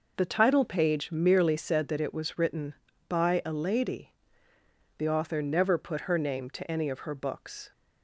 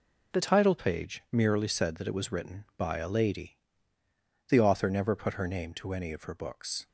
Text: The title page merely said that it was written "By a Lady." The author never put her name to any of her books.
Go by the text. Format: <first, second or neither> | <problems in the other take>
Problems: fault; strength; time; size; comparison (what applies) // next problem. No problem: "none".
first | changes voice at "title"; from 0.4 s on; 6.4 s long